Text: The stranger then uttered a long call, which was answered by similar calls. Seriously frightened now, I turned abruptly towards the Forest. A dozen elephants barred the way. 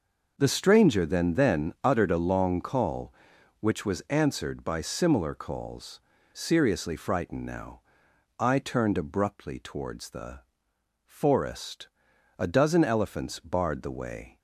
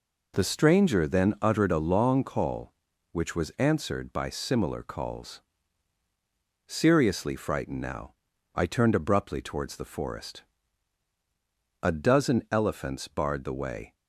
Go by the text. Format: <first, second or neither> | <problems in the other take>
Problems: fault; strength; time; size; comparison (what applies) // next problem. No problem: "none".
second | says "then" twice; at 1.3 s // pauses between "the" and "Forest"; noticeable; at 10.4 s; 0.64 s long